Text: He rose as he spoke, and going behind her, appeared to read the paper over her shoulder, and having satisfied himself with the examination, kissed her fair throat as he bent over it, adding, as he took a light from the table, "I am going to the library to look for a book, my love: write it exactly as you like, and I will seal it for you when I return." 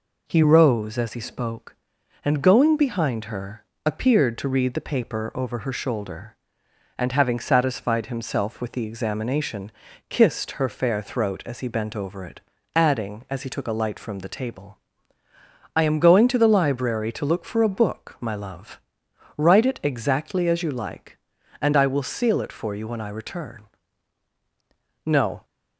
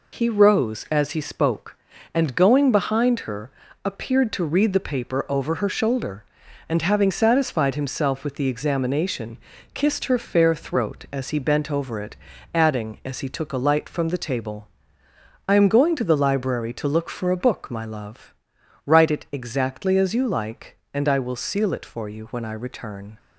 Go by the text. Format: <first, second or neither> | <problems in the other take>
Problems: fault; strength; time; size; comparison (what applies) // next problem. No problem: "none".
second | goes on to say "No"; slight; from 25.0 s on; 0.40 s long